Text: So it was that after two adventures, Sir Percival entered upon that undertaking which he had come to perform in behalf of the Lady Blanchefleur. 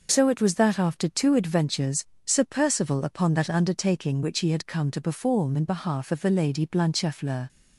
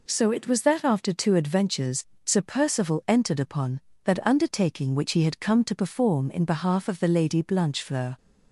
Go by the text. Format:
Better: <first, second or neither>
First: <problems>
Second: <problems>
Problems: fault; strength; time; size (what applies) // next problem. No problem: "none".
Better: second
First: skips "entered"; at 3.0 s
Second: none